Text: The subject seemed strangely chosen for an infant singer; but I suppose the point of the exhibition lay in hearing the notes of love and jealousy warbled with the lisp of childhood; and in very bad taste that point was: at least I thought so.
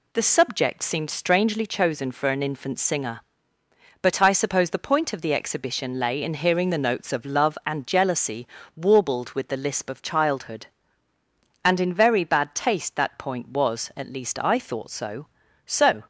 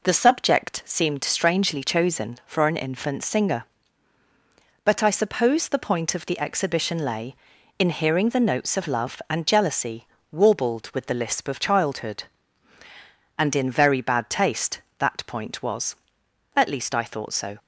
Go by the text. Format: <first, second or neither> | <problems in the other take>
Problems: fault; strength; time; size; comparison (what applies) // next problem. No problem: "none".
second | pauses between "jealousy" and "warbled"; slight; at 8.4 s; 0.28 s long; slight in the second // says "so" twice; at 15.6 s